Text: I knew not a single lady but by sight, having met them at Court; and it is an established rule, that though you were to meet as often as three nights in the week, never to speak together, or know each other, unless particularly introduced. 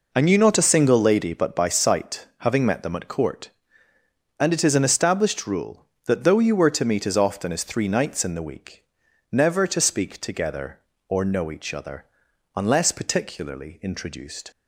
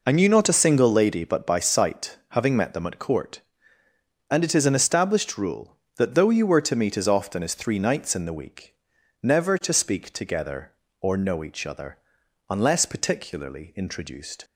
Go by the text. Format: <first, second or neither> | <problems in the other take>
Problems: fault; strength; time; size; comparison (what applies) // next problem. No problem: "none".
neither | none